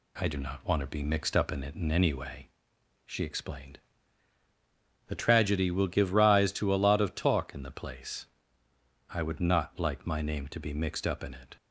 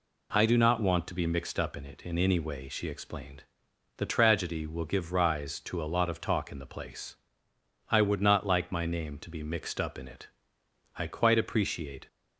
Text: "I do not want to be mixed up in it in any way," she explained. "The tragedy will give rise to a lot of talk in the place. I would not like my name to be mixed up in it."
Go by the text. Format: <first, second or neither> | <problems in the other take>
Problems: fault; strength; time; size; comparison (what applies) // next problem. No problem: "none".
first | goes on to say "I quite appreciate"; noticeable; from 10.9 s on; 1.1 s long